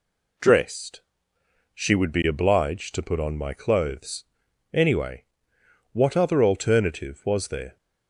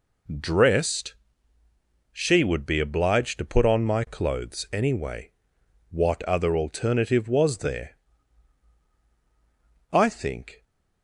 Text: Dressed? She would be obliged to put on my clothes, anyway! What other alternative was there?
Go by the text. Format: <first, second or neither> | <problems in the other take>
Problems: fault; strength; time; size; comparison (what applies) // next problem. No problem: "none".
first | goes on to say "I think"; noticeable; from 9.9 s on; 0.74 s long